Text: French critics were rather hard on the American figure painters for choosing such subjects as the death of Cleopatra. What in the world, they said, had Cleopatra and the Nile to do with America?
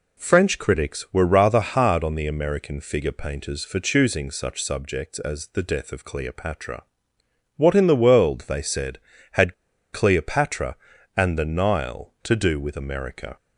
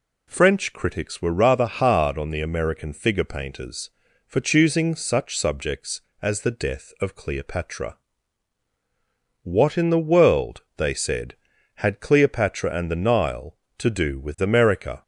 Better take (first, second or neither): second